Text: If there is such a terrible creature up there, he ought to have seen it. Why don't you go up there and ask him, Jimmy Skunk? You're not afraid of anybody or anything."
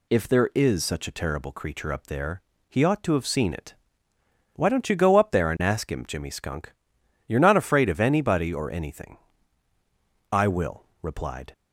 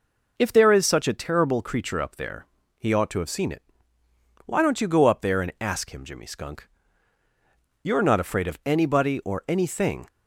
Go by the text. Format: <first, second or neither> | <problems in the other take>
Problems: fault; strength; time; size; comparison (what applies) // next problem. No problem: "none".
second | goes on to say "I will replied"; noticeable; from 10.3 s on; 1.2 s long